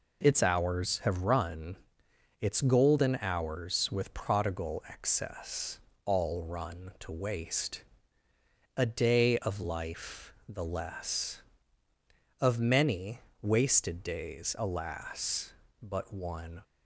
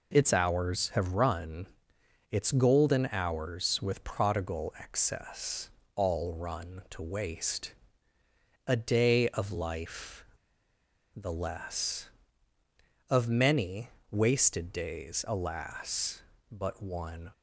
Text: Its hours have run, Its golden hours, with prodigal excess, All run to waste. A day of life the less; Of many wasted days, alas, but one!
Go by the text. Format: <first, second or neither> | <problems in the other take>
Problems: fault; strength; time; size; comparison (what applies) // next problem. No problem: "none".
first | pauses between "life" and "the"; noticeable; at 10.2 s; 0.88 s long // pauses between "many" and "wasted"; slight; at 13.9 s; 0.20 s long; slight in the first